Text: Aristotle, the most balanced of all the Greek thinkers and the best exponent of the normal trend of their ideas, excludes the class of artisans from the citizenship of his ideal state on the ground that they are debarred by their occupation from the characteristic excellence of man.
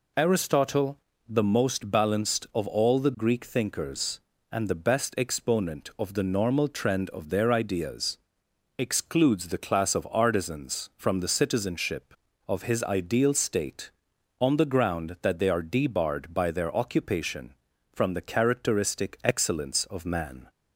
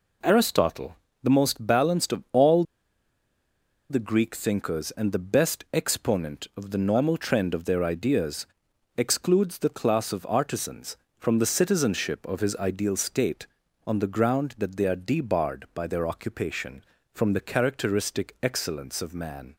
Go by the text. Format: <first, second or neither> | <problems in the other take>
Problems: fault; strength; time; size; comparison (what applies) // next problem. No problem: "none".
first | pauses between "all" and "the"; strong; at 2.6 s; 1.2 s long